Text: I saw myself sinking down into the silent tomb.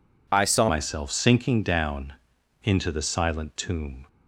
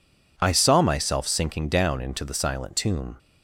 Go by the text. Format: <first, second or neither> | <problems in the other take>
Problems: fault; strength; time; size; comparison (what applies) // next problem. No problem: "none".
second | changes voice at "myself"; from 0.6 s on; 3.4 s long // pauses between "down" and "into"; noticeable; at 2.1 s; 0.54 s long